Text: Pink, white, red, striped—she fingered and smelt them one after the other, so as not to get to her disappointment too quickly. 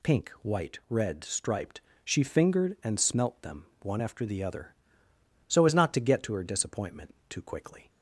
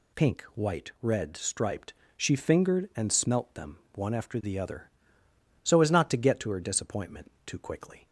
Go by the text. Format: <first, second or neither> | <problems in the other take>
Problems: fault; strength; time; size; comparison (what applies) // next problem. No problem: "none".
neither | pauses between "them" and "one"; slight; the same in both